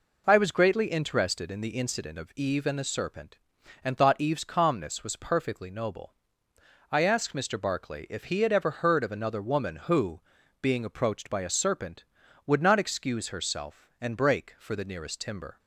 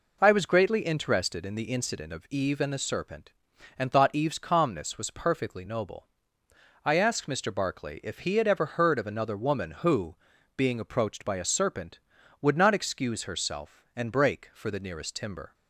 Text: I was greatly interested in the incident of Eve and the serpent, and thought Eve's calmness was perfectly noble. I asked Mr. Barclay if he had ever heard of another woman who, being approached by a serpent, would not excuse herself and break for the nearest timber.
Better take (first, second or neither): neither